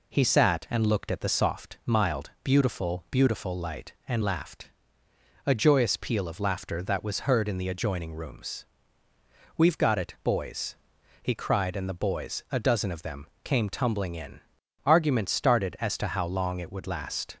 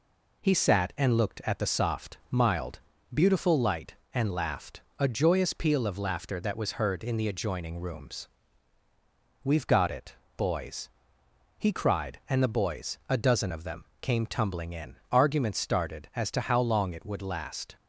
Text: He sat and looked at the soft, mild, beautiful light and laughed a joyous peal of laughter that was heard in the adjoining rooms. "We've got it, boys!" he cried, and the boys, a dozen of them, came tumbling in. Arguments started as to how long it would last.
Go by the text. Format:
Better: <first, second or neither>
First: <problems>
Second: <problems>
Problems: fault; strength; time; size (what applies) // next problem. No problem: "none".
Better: second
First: says "beautiful" twice; at 3.1 s // pauses between "laughed" and "a"; noticeable; at 4.7 s; 0.74 s long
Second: pauses between "laughed" and "a"; slight; at 4.7 s; 0.18 s long